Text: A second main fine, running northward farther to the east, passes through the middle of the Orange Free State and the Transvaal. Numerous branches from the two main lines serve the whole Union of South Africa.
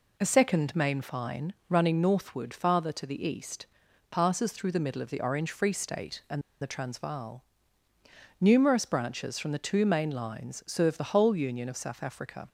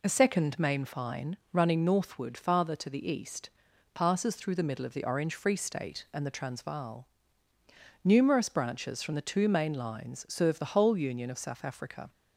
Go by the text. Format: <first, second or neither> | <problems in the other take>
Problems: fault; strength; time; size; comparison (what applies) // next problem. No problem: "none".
second | pauses between "and" and "the"; slight; at 6.4 s; 0.20 s long